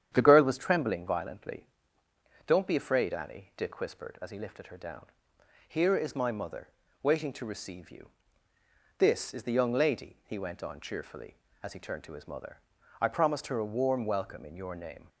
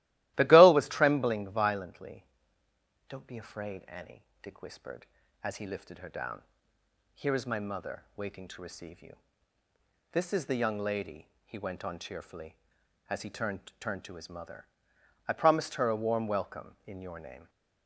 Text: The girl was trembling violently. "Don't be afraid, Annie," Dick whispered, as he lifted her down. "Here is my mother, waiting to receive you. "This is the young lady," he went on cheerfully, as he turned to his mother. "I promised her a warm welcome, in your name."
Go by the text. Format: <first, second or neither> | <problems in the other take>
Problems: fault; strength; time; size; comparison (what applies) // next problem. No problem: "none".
first | starts louder than the rest; strong; until 1.3 s; 16 dB; strong in the first // says "turned" twice; at 13.8 s